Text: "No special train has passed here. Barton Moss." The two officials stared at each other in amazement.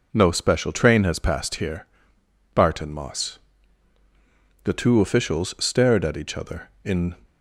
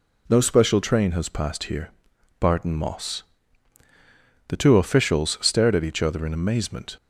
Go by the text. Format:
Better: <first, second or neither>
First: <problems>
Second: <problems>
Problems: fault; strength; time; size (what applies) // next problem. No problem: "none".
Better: second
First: stops before "amazement"; at 7.2 s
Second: none